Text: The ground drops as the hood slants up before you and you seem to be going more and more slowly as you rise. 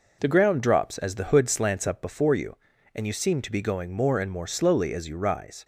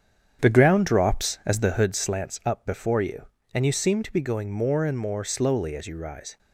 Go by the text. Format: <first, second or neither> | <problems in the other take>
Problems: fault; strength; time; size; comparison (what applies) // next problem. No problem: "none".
first | starts louder than the rest; strong; until 2.0 s; 8 dB